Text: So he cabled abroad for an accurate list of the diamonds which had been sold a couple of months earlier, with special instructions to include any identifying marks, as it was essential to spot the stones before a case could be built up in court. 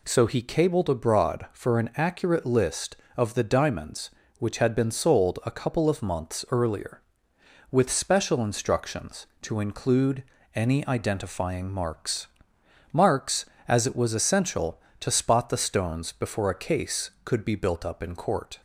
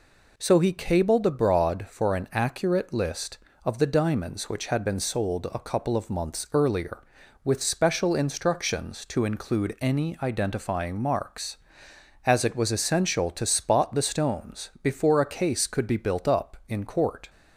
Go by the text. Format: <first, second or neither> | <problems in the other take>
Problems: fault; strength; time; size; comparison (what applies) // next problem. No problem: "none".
second | pauses between "include" and "any"; slight; at 10.2 s; 0.32 s long // says "marks" twice; at 12.9 s